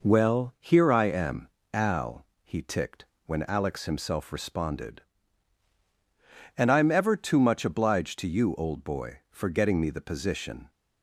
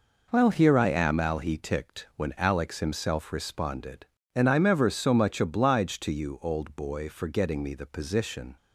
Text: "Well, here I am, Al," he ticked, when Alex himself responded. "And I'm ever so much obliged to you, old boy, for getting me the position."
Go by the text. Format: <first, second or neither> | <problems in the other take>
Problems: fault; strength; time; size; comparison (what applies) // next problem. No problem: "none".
second | says "too" for "so"; at 7.1 s